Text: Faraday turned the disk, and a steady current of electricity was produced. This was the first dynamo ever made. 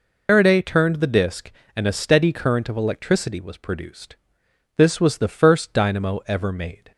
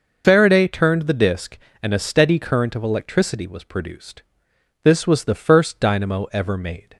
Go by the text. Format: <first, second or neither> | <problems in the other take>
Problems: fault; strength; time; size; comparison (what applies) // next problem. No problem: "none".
second | loses the start of "Faraday"; at 0.2 s; 105 ms